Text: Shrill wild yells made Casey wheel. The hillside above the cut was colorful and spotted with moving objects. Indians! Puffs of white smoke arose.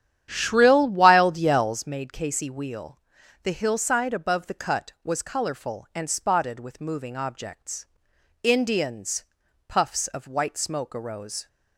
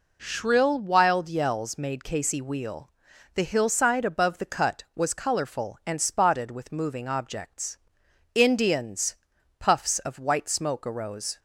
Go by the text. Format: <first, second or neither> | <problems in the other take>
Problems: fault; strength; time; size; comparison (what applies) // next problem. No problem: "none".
second | starts louder than the rest; strong; until 1.9 s; 10 dB